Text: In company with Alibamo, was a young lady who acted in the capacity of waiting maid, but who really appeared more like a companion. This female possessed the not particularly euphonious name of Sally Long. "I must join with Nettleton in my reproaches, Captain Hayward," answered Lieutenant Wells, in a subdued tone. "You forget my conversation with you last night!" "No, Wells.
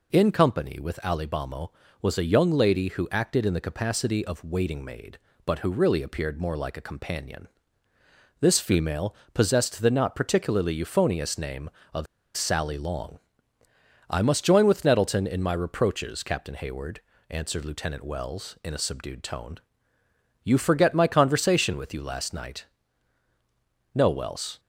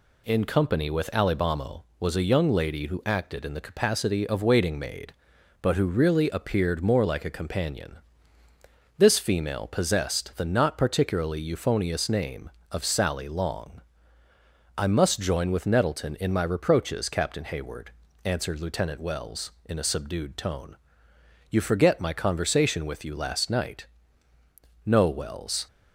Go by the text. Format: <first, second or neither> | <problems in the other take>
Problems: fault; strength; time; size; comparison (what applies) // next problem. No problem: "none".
second | pauses between "female" and "possessed"; slight; at 9.1 s; 0.18 s long // pauses between "of" and "Sally"; slight; at 12.0 s; 0.31 s long